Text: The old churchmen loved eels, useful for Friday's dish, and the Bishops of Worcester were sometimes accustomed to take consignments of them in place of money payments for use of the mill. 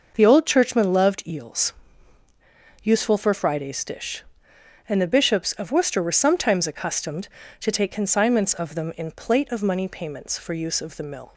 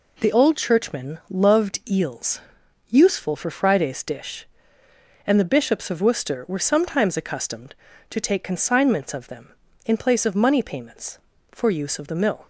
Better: second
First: says "plate" for "place"; at 9.1 s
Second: none

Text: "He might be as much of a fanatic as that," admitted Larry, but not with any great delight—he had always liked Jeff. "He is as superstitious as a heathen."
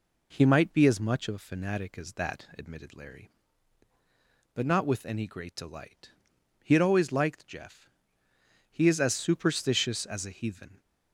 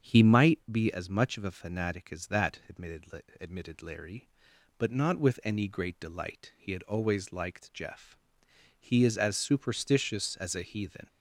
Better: first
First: none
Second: starts louder than the rest; strong; until 1.1 s; 7.5 dB // says "admitted" twice; at 3.3 s

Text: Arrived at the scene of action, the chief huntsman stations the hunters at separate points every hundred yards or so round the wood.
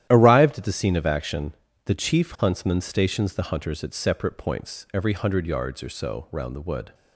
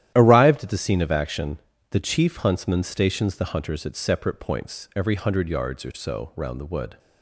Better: neither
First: starts louder than the rest; strong; until 1.1 s; 11.5 dB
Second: starts louder than the rest; strong; until 1.1 s; 12 dB

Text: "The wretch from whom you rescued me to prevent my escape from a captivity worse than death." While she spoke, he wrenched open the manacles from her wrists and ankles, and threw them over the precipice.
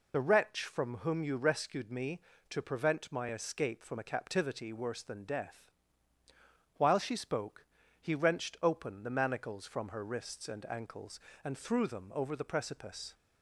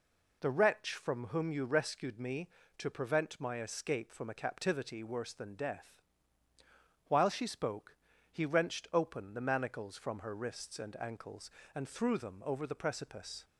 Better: second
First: loses the start of "The"; at 0.1 s; 25 ms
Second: none

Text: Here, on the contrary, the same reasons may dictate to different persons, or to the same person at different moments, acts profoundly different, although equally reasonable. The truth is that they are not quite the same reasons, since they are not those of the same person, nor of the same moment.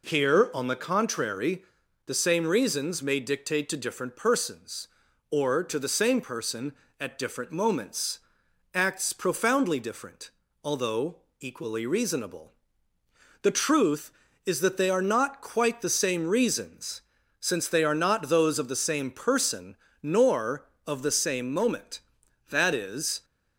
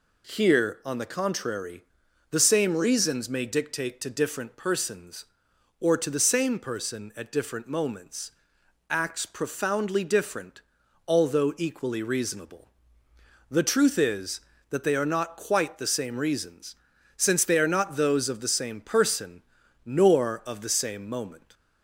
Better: second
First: pauses between "although" and "equally"; slight; at 11.2 s; 0.20 s long // goes on to say "That is"; noticeable; from 22.5 s on; 0.74 s long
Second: none

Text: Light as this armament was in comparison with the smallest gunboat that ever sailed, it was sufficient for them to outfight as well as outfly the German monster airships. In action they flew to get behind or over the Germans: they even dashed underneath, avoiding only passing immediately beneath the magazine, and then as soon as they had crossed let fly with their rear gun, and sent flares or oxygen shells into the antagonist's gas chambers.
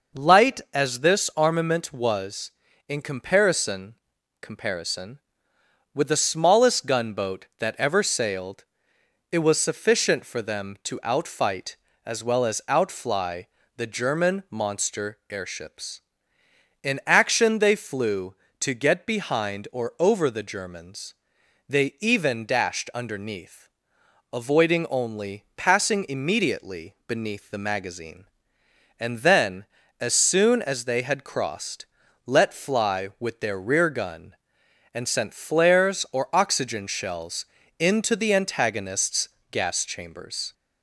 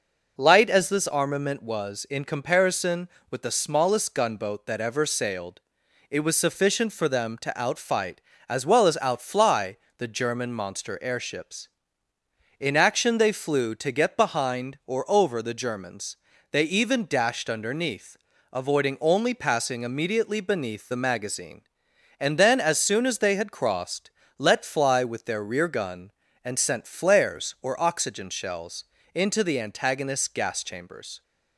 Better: second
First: says "comparison" twice; at 4.4 s // pauses between "outfly" and "the"; slight; at 13.4 s; 0.30 s long // pauses between "crossed" and "let"; at 31.8 s; 0.40 s long // pauses between "shells" and "into"; slight; at 37.4 s; 0.34 s long // pauses between "antagonist's" and "gas"; slight; at 39.2 s; 0.22 s long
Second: pauses between "outfly" and "the"; slight; at 9.7 s; 0.20 s long // pauses between "crossed" and "let"; slight; at 24.1 s; 0.26 s long // pauses between "shells" and "into"; slight; at 28.8 s; 0.30 s long

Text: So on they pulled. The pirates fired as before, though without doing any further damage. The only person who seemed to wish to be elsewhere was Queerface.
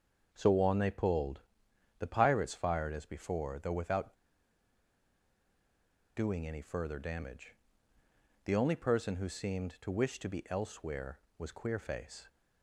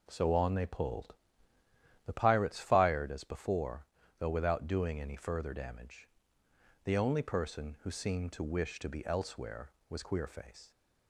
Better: second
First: starts louder than the rest; until 1.3 s; 6.5 dB // pauses between "without" and "doing"; strong; at 4.1 s; 2.0 s long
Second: none

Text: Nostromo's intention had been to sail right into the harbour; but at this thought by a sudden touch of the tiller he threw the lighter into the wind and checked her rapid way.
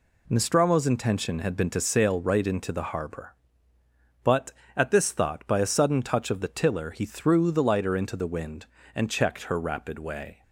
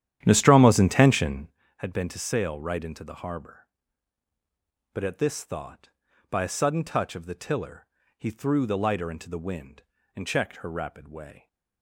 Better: first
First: none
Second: starts louder than the rest; strong; until 1.6 s; 11 dB // pauses between "tiller" and "he"; slight; at 7.8 s; 0.32 s long

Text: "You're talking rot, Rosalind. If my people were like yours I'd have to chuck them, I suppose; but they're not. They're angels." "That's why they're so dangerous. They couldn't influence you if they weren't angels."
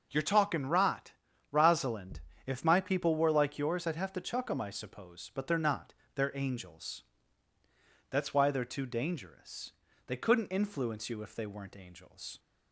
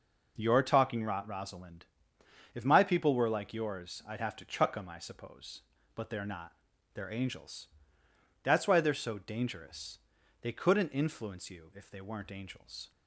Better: second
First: says "too" for "so"; at 8.6 s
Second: none

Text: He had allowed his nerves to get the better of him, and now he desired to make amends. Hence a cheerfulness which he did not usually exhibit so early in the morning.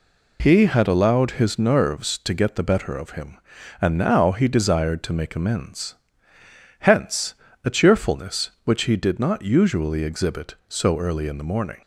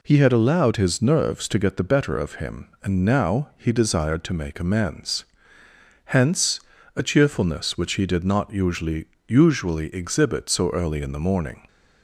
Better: first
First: pauses between "Hence" and "a"; slight; at 7.3 s; 0.28 s long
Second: pauses between "Hence" and "a"; slight; at 6.5 s; 0.36 s long // says "usually" twice; at 9.2 s

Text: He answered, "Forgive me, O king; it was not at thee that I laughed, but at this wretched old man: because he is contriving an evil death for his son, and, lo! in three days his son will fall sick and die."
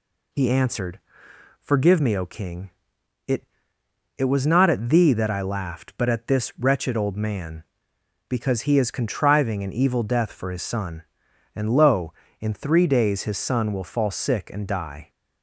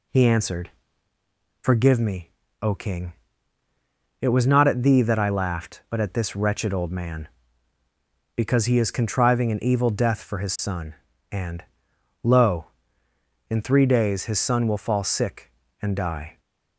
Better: second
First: says "it" twice; at 4.1 s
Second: none

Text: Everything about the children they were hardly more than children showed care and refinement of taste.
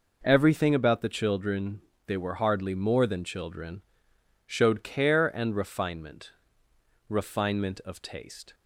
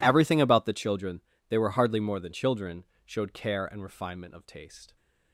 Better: second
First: pauses between "children" and "they"; slight; at 1.7 s; 0.26 s long // pauses between "children" and "showed"; noticeable; at 3.8 s; 0.64 s long // says "refinement" twice; at 7.0 s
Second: pauses between "children" and "they"; slight; at 1.2 s; 0.28 s long // pauses between "children" and "showed"; slight; at 2.8 s; 0.20 s long

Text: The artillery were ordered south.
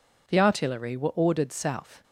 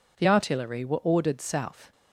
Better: neither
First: none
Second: none

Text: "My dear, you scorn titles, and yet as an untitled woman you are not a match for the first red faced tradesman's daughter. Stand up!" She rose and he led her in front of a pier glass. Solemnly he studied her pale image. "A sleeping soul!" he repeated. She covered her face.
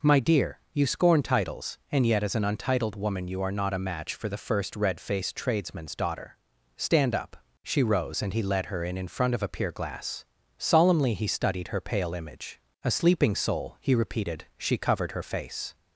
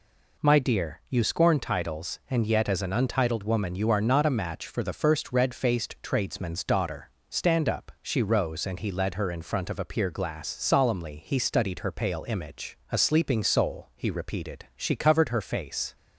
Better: second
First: says "in" twice; at 8.9 s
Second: none

